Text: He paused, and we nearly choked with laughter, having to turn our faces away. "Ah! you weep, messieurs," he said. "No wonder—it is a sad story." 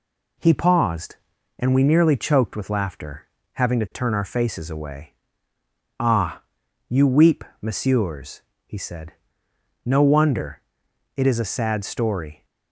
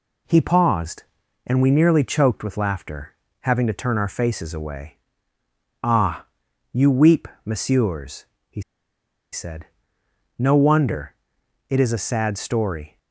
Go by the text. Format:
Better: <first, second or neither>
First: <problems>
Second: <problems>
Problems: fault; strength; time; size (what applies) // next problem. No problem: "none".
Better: first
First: none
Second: pauses between "he" and "said"; noticeable; at 8.6 s; 0.72 s long